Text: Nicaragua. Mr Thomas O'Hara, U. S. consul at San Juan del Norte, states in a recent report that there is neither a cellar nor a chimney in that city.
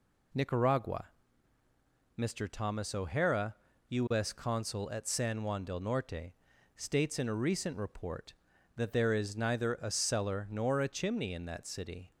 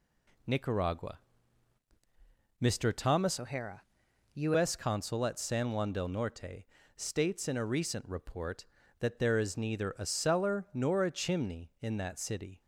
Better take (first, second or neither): first